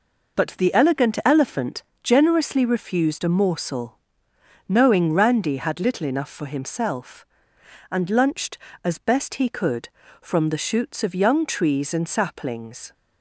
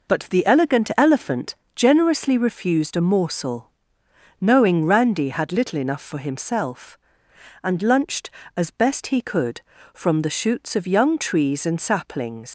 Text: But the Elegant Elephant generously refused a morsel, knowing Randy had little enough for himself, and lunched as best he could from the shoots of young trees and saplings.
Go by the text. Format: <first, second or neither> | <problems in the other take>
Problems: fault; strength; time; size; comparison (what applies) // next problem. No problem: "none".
first | pauses between "Elephant" and "generously"; slight; at 1.5 s; 0.20 s long; slight in the first // leaves "saplings" unfinished; at 12.4 s; 115 ms